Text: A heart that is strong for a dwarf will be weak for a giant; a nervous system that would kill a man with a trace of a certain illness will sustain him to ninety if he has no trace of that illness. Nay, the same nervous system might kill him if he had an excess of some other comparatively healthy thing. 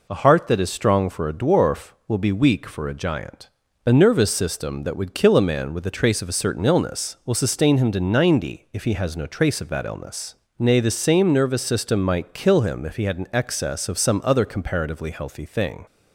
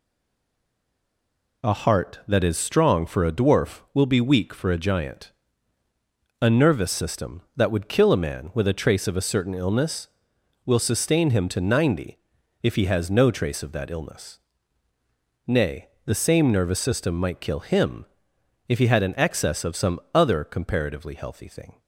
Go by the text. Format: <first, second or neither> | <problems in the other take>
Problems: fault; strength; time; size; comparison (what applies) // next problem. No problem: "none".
first | stays silent before the first word; noticeable; until 1.6 s; 1.6 s long // pauses between "ninety" and "if"; at 12.1 s; 0.44 s long // pauses between "him" and "if"; noticeable; at 18.0 s; 0.64 s long // pauses between "some" and "other"; slight; at 19.9 s; 0.16 s long